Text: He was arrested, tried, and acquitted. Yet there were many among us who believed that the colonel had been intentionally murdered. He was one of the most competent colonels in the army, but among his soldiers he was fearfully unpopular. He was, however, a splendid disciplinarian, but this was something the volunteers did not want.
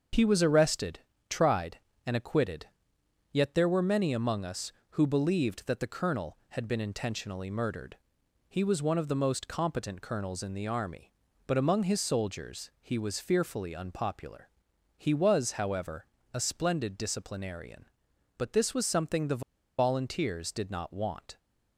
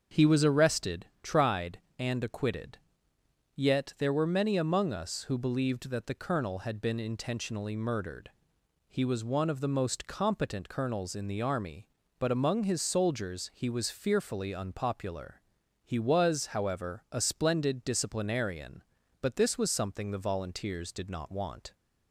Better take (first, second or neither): second